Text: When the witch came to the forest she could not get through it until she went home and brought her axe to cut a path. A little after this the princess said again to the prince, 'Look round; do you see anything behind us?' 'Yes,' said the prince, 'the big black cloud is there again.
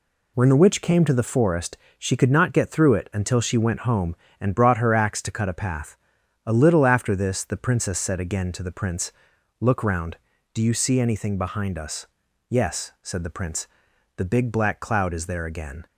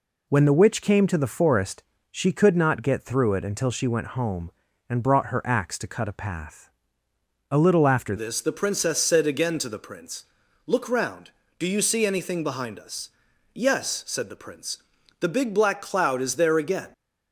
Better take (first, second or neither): first